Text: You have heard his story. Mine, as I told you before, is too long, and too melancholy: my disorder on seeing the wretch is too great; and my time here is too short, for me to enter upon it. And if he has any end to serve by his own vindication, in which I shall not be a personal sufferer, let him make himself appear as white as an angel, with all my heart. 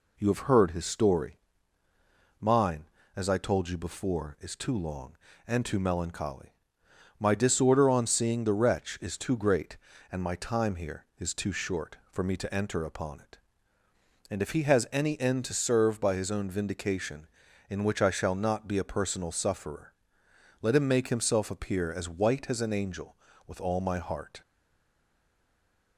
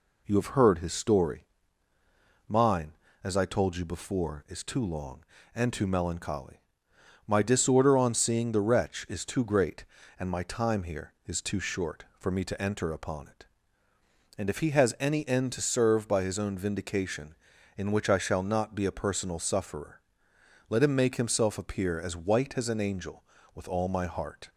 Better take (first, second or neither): second